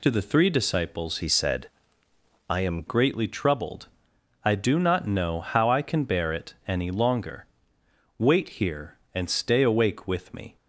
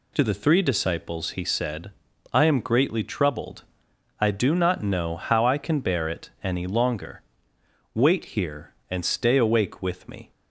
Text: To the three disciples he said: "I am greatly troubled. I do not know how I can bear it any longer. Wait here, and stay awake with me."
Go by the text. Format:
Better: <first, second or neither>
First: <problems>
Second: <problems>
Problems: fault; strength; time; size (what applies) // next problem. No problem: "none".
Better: second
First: changes voice from "he" to "am"; from 1.2 to 2.8 s; 1.6 s long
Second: none